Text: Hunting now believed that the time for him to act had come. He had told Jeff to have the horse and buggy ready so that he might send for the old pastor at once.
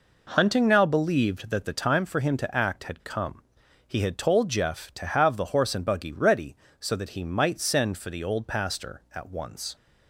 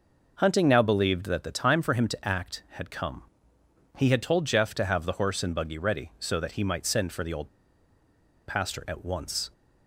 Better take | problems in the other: first | pauses between "old" and "pastor"; at 7.4 s; 0.99 s long

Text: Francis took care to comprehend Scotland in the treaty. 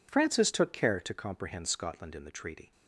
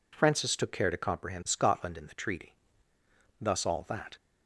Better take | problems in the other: first | goes on to say "Thus all that"; noticeable; from 3.3 s on; 0.78 s long

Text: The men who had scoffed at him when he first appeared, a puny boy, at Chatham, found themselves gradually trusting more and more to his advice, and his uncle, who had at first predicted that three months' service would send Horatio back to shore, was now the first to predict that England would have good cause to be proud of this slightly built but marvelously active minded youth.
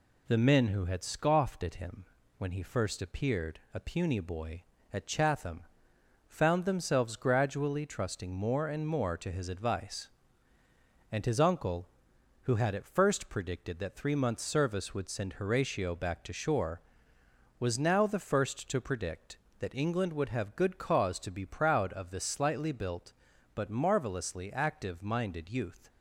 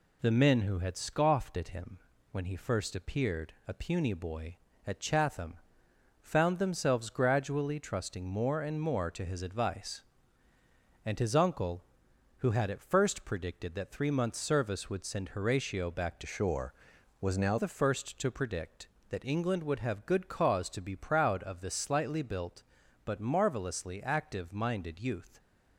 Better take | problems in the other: first | pauses between "him" and "when"; slight; at 1.9 s; 0.32 s long; slight in the first // changes voice from "shore" to "now"; from 16.2 to 17.5 s; 1.3 s long

